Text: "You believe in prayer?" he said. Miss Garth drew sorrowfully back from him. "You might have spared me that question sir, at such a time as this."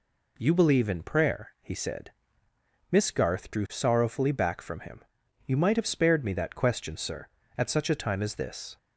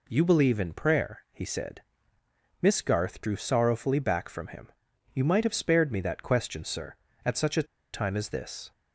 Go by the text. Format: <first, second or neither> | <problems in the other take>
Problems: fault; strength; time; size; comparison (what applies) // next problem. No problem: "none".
first | pauses between "a" and "time"; slight; at 7.6 s; 0.28 s long